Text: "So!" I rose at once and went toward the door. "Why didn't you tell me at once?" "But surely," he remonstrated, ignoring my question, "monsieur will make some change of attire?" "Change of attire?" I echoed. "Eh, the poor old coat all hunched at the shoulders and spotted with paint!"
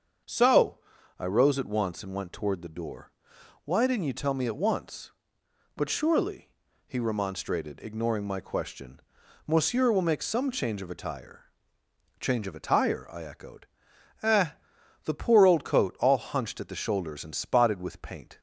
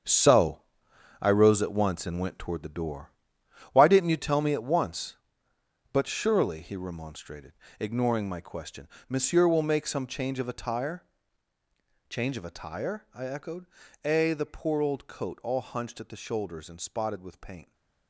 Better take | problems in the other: first | gets quieter; strong; throughout; 11 dB // starts louder than the rest; strong; until 1.6 s; 7.5 dB; also in the first

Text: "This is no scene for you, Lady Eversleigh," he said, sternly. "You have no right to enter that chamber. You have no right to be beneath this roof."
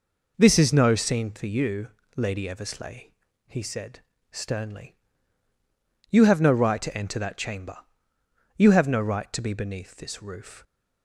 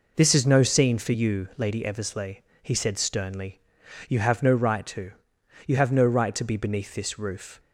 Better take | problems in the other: first | skips "enter that chamber"; at 5.3 s

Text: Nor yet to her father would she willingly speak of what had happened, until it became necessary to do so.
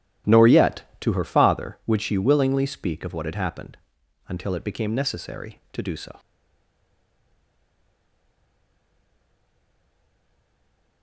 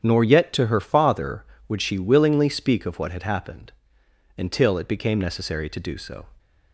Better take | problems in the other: second | starts louder than the rest; strong; until 1.4 s; 13 dB; strong in the second // stays silent after the last word; strong; from 6.1 s on; 4.9 s long

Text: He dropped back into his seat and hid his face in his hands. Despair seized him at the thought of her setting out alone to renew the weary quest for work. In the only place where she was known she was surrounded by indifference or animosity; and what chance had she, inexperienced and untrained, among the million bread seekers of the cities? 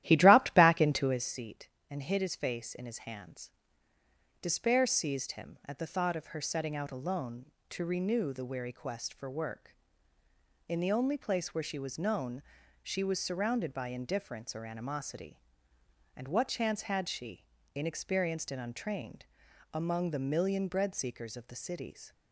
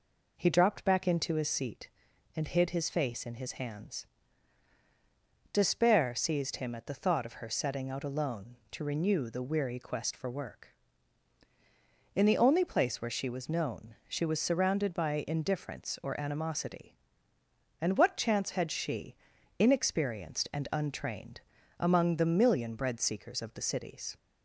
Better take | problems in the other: second | starts louder than the rest; strong; until 1.3 s; 13.5 dB // pauses between "known" and "she"; at 12.4 s; 0.40 s long

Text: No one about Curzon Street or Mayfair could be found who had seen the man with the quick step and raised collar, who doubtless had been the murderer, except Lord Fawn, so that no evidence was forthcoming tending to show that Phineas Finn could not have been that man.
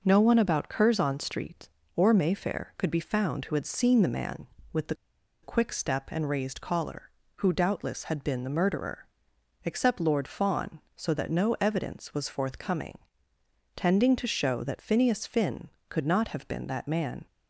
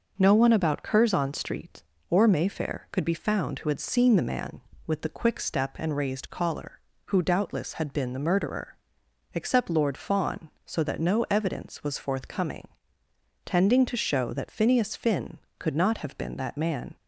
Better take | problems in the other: second | pauses between "the" and "quick"; noticeable; at 4.9 s; 0.48 s long // pauses between "forthcoming" and "tending"; noticeable; at 12.9 s; 0.78 s long; noticeable in the second

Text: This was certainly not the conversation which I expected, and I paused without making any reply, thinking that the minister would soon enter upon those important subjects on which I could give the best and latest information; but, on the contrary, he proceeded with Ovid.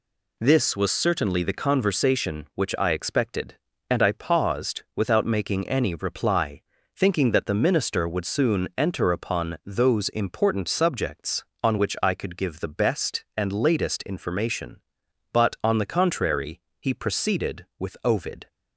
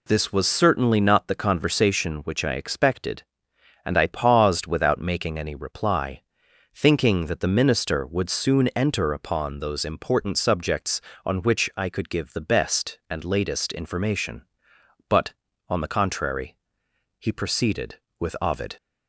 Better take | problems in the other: second | skips "not"; at 1.4 s

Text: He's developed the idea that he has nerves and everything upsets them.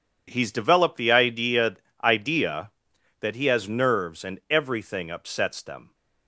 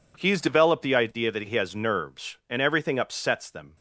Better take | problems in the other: second | says "idea" twice; at 2.0 s

